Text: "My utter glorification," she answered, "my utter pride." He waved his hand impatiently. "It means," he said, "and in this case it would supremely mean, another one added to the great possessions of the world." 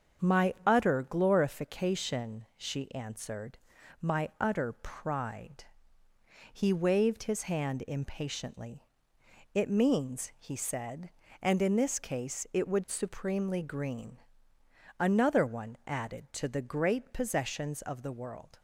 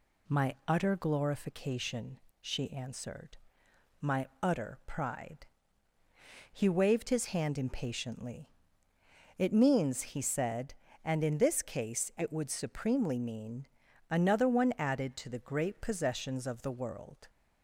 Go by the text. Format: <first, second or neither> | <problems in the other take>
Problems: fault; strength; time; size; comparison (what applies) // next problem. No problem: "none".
second | starts louder than the rest; strong; until 1.3 s; 7.5 dB // says "green" for "mean"; at 13.6 s